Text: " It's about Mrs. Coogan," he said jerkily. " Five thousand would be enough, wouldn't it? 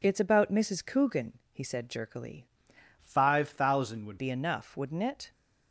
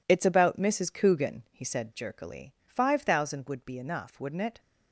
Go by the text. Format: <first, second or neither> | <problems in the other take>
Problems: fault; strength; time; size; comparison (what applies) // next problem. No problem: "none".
second | changes voice from "Five" to "would"; from 3.0 to 4.1 s; 1.1 s long